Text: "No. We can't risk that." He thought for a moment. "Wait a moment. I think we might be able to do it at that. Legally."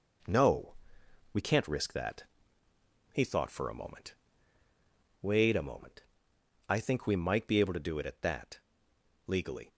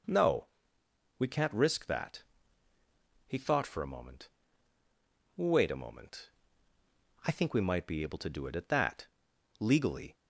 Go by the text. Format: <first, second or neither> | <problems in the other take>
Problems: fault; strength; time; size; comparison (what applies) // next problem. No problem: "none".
second | gets quieter; noticeable; throughout; 5 dB